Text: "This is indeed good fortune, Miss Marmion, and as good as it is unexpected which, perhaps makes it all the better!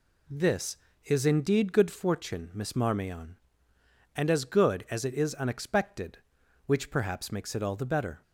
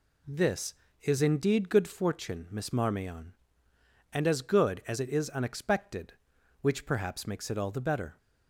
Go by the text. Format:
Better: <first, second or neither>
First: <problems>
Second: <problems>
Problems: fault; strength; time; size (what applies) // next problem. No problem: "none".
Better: neither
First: none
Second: none